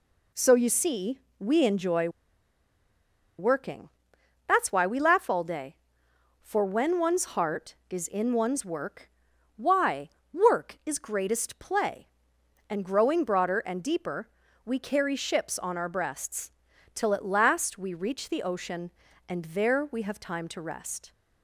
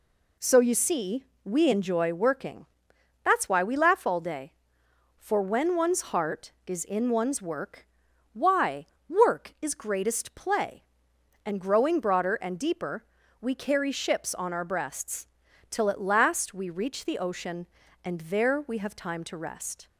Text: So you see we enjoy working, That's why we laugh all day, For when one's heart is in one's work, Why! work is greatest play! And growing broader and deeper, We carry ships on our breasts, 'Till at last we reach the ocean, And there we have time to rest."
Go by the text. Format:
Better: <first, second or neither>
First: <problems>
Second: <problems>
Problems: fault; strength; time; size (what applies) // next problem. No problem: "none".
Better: second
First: pauses between "see" and "we"; slight; at 1.1 s; 0.20 s long // pauses between "enjoy" and "working"; strong; at 2.0 s; 1.3 s long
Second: pauses between "see" and "we"; slight; at 1.2 s; 0.20 s long